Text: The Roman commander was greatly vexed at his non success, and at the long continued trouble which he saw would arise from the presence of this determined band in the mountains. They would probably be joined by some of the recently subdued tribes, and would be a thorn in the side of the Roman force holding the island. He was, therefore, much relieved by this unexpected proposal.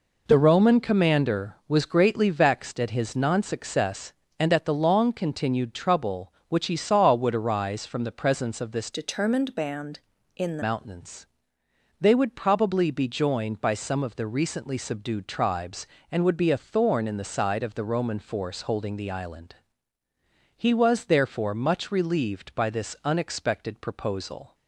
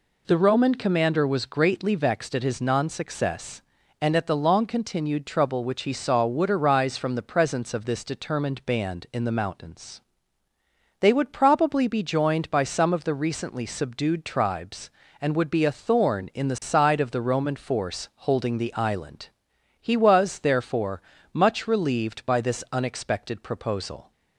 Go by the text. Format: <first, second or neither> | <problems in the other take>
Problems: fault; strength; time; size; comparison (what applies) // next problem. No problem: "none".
second | changes voice from "determined" to "the"; from 8.9 to 10.6 s; 1.7 s long